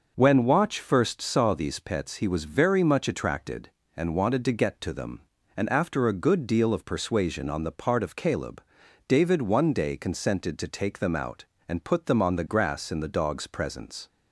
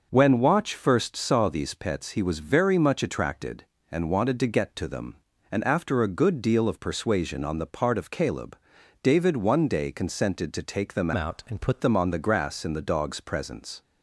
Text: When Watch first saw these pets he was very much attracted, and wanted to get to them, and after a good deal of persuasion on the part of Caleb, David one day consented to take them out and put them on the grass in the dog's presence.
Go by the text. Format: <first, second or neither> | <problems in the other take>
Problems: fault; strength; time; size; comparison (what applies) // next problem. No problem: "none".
first | changes voice from "out" to "put"; from 11.1 to 11.8 s; 0.7 s long